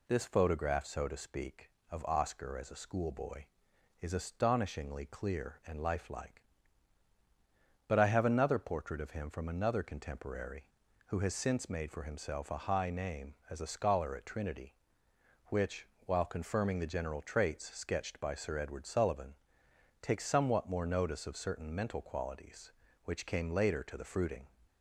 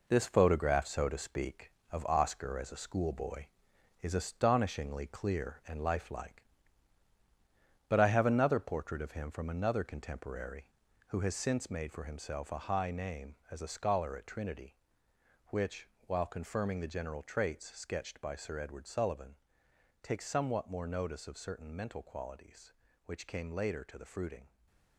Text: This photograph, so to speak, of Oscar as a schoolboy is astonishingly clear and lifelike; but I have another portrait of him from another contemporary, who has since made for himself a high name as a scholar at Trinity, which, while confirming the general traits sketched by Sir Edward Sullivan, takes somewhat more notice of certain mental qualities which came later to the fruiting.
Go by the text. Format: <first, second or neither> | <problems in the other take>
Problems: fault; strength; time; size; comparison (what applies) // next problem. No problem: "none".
first | gets quieter; strong; throughout; 7 dB // stays silent after the last word; slight; from 24.4 s on; 0.5 s long